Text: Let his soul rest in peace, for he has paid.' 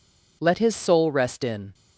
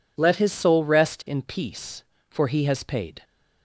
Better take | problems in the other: second | stops before "peace for he has paid"; at 1.7 s

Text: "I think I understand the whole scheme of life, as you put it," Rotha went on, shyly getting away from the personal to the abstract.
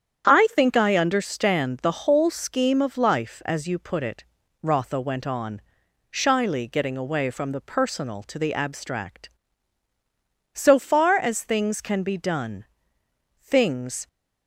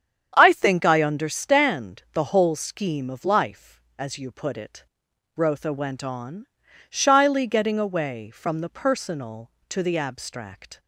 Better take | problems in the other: second | starts louder than the rest; strong; until 1.2 s; 8.5 dB; strong in the second // goes on to say "So far as things can be done things"; strong; from 10.5 s on; 3.5 s long

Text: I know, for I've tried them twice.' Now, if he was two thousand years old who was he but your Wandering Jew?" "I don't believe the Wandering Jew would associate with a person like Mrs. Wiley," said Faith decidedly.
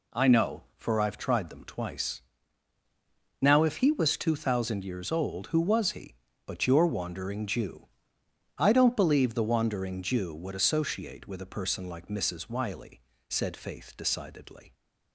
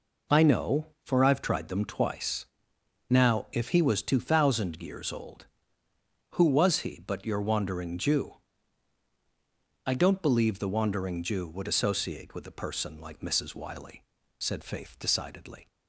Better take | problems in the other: neither | none

